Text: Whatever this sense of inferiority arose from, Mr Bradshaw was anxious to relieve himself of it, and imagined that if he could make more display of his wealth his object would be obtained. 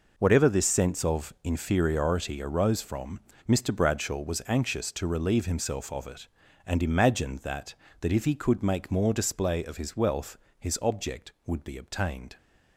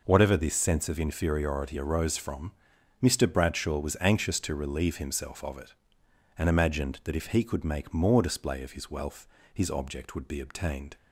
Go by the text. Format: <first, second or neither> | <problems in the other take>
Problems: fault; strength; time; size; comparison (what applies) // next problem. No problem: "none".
second | says "that" twice; at 7.9 s // pauses between "wealth" and "his"; slight; at 10.3 s; 0.24 s long; slight in the second